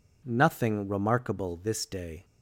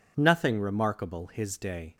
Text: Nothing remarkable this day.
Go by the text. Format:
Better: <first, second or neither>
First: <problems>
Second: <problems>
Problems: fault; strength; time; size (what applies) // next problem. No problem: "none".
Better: first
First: none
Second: says "his" for "this"; at 1.2 s